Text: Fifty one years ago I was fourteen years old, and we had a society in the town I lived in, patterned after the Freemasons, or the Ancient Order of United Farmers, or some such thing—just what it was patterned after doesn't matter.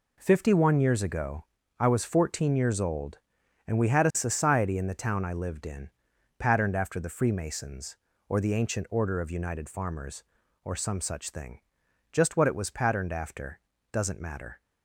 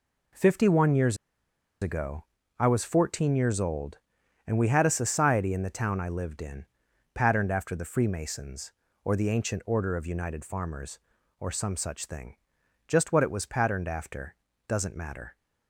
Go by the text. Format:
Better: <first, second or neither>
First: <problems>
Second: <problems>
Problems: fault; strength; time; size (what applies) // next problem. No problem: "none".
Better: first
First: pauses between "ago" and "I"; slight; at 1.4 s; 0.34 s long // pauses between "after" and "doesn't"; slight; at 13.5 s; 0.32 s long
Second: pauses between "years" and "ago"; noticeable; at 1.1 s; 0.65 s long // pauses between "ago" and "I"; slight; at 2.2 s; 0.34 s long // pauses between "after" and "doesn't"; slight; at 14.3 s; 0.32 s long